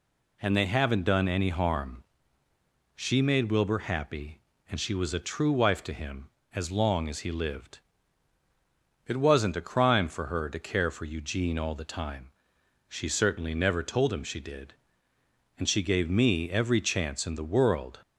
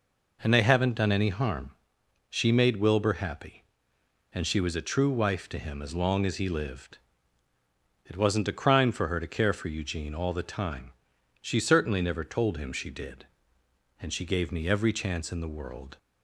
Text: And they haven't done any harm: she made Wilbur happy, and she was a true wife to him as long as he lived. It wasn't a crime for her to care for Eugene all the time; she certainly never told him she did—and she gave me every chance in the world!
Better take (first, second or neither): neither